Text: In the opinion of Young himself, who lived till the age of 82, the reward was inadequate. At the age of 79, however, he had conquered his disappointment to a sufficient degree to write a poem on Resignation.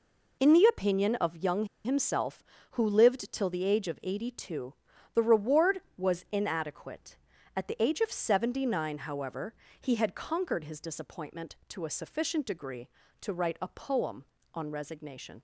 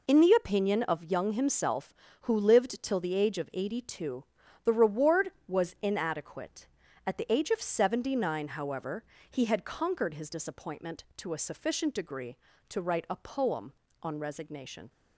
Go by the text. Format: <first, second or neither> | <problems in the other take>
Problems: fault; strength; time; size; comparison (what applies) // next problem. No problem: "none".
second | pauses between "Young" and "himself"; slight; at 1.6 s; 0.18 s long